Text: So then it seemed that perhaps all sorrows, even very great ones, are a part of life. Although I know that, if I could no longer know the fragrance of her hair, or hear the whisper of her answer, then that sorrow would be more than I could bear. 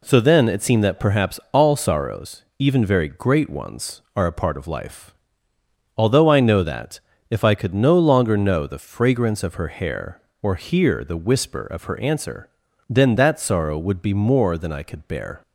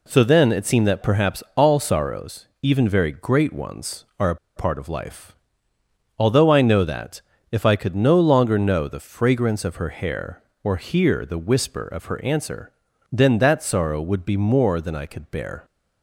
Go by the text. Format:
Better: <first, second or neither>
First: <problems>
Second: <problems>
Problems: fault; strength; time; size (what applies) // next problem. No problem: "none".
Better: first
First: none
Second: pauses between "a" and "part"; slight; at 4.3 s; 0.19 s long